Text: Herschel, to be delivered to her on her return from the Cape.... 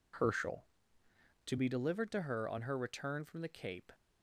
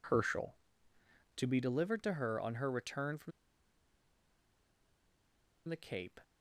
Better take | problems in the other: first | pauses between "from" and "the"; strong; at 3.3 s; 2.3 s long

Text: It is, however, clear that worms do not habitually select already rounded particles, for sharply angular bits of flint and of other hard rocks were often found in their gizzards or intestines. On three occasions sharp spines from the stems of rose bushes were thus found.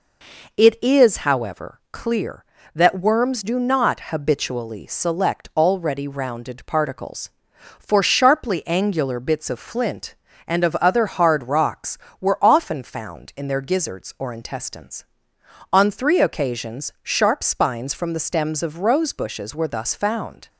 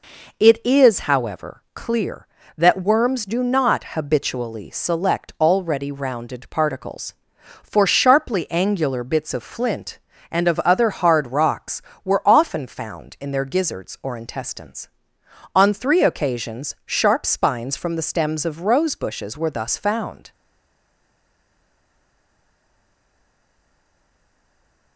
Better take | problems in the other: first | stays silent after the last word; strong; from 20.3 s on; 4.6 s long

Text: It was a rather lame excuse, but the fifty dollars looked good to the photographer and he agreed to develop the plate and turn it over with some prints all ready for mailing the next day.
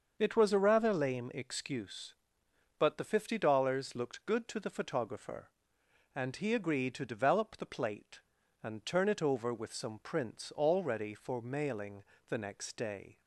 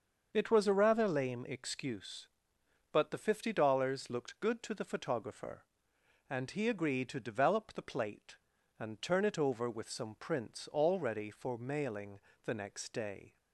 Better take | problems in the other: neither | starts louder than the rest; the same in both // pauses between "mailing" and "the"; slight; the same in both

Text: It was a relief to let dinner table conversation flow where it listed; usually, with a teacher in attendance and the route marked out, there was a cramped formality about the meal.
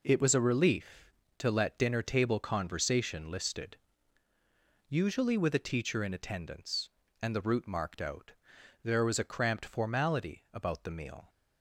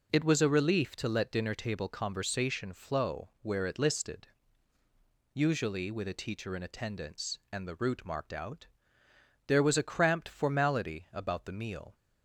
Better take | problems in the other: second | skips "flow where it"; at 3.3 s

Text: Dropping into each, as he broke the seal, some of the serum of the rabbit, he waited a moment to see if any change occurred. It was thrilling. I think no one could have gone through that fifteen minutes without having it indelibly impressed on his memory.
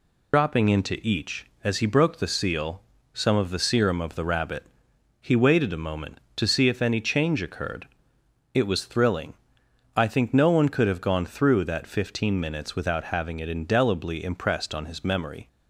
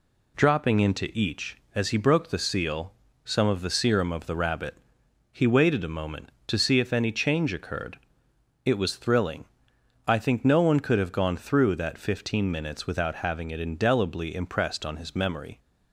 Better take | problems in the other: second | loses the start of "Dropping"; at 0.3 s; 95 ms

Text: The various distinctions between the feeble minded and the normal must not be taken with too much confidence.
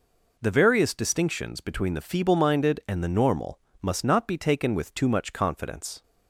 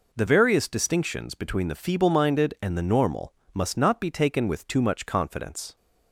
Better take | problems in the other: neither | pauses between "normal" and "must"; slight; the same in both

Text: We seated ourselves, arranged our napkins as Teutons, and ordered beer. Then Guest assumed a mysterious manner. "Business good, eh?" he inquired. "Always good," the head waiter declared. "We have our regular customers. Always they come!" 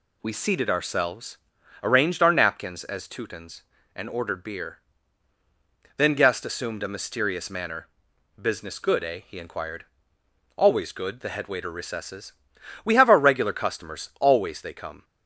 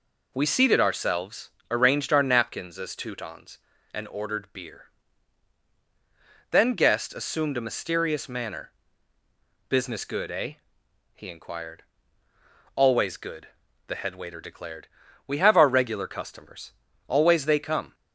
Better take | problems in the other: second | says "recesses" for "declared"; at 11.7 s

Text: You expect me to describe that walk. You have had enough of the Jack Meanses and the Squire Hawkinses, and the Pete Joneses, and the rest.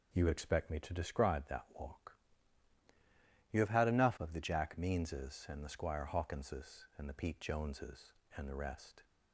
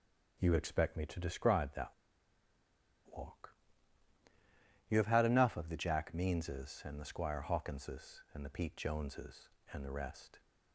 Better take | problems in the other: first | pauses between "that" and "walk"; at 1.9 s; 1.2 s long

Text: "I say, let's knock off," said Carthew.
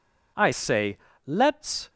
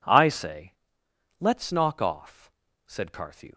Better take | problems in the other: second | stops before "knock off said Carthew"; at 1.8 s

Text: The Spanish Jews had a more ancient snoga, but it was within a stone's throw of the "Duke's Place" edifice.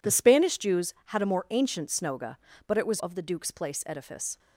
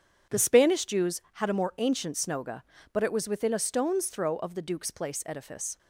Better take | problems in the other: second | skips "within a stone's throw"; at 2.9 s

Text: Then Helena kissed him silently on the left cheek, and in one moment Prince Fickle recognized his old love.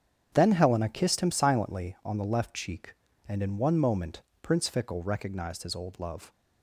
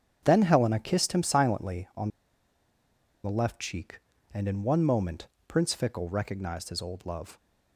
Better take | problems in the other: first | starts louder than the rest; strong; until 1.2 s; 8 dB; strong in the first // pauses between "on" and "the"; at 2.0 s; 1.1 s long // pauses between "moment" and "Prince"; slight; at 5.2 s; 0.20 s long; slight in the first

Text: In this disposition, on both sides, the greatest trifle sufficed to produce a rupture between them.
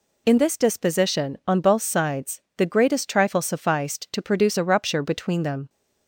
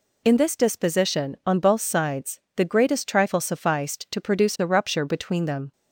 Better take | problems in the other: neither | none

